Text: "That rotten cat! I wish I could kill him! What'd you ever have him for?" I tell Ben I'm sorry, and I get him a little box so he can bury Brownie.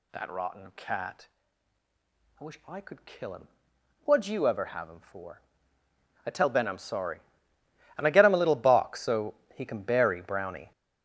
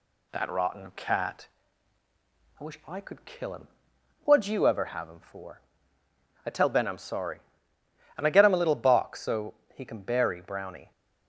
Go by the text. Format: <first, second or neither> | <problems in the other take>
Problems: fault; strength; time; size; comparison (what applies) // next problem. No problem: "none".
second | gets louder; strong; throughout; 10 dB // pauses between "so" and "he"; slight; at 9.3 s; 0.18 s long; slight in the second